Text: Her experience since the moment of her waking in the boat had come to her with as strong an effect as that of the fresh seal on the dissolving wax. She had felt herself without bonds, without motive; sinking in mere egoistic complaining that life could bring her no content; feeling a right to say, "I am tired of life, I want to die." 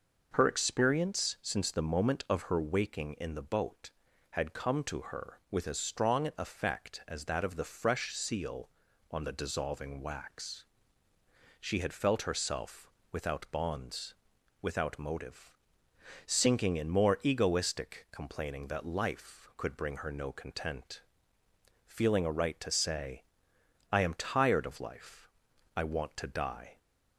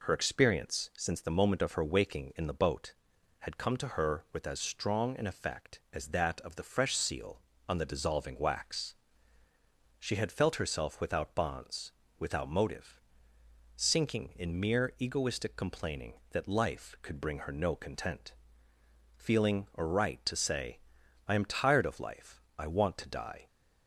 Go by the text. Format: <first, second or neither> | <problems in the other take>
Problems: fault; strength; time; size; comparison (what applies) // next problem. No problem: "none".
second | pauses between "herself" and "without"; slight; at 12.9 s; 0.22 s long // says "more" for "mere"; at 16.8 s